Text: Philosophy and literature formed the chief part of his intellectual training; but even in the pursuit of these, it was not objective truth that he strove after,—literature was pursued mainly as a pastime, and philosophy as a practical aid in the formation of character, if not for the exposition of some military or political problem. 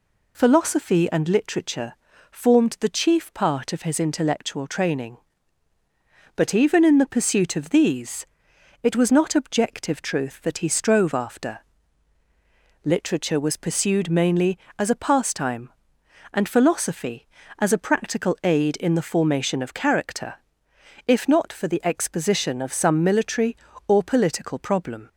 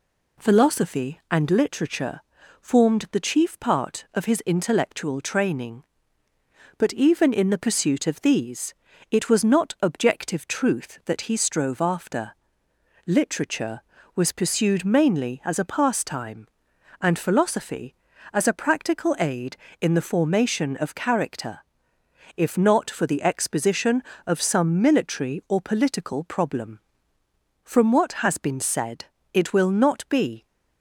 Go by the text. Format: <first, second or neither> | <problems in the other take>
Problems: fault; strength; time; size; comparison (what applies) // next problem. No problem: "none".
first | pauses between "literature" and "formed"; at 2.2 s; 0.40 s long; slight in the first // goes on to say "From what has been said it will not be"; strong; from 27.6 s on; 2.8 s long